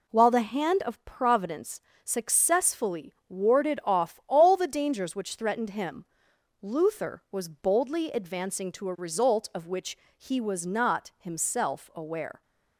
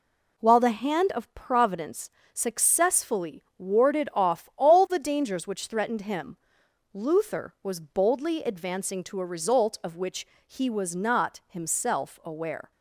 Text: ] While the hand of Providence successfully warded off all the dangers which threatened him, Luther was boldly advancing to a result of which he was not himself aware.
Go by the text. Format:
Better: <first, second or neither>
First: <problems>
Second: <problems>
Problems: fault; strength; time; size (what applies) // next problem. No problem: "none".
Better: neither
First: pauses between "Providence" and "successfully"; slight; at 1.8 s; 0.24 s long // pauses between "which" and "he"; slight; at 9.9 s; 0.22 s long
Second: pauses between "Providence" and "successfully"; slight; at 2.1 s; 0.24 s long // pauses between "which" and "he"; slight; at 10.2 s; 0.22 s long